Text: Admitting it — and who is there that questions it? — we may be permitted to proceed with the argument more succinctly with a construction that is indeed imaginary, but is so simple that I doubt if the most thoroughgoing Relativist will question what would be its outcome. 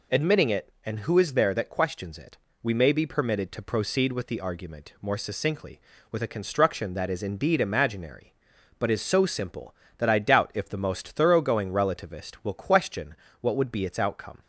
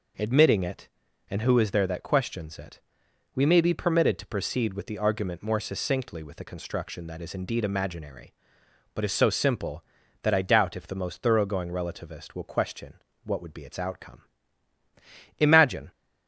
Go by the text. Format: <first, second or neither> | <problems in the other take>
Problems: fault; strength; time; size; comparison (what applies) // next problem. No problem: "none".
first | pauses between "question" and "what"; slight; at 12.9 s; 0.30 s long; slight in the first // goes on to say "Imagine"; from 15.4 s on; 0.50 s long